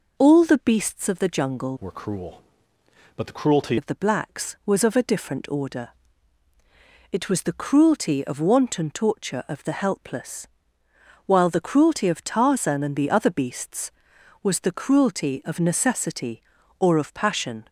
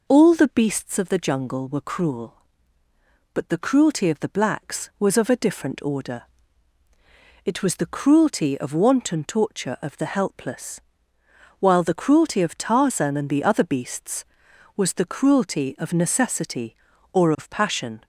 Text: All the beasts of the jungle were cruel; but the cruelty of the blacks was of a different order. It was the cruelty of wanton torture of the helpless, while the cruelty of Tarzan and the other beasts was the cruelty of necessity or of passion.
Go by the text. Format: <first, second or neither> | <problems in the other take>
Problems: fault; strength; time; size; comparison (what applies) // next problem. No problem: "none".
second | changes voice from "were" to "cruelty"; from 1.8 to 3.7 s; 1.9 s long